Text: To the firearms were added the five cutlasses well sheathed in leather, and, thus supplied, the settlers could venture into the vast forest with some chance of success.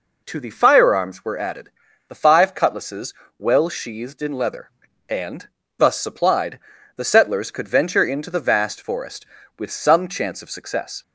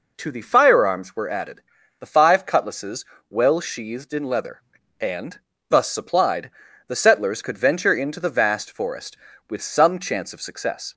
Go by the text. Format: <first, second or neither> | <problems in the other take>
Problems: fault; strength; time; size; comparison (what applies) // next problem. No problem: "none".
neither | pauses between "added" and "the"; the same in both // pauses between "cutlasses" and "well"; slight; the same in both